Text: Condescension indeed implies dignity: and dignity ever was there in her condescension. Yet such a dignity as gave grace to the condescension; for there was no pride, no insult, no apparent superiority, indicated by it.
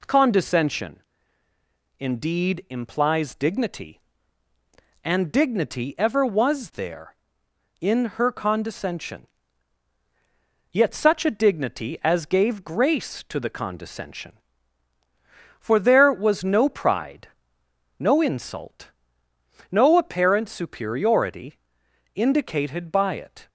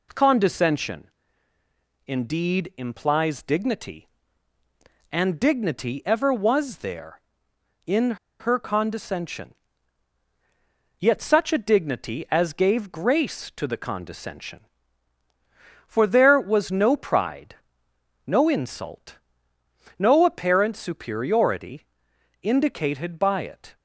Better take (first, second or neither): first